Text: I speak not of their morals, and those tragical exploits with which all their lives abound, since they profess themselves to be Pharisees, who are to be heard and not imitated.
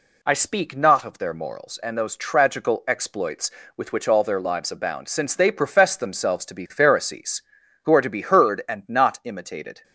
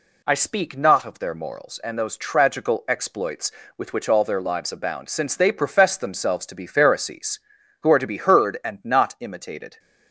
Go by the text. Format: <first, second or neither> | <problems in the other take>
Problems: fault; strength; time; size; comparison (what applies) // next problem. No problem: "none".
neither | none